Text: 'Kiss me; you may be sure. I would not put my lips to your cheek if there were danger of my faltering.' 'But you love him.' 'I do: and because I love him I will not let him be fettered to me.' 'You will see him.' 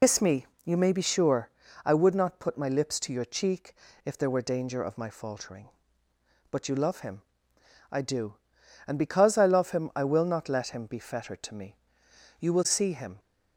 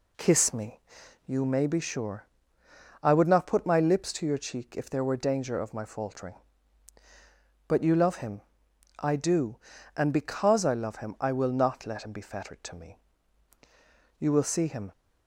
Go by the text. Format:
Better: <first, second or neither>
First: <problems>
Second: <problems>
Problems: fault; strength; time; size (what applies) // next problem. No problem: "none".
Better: second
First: loses the start of "Kiss"; at 0.0 s; 100 ms // pauses between "cheek" and "if"; slight; at 3.7 s; 0.30 s long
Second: none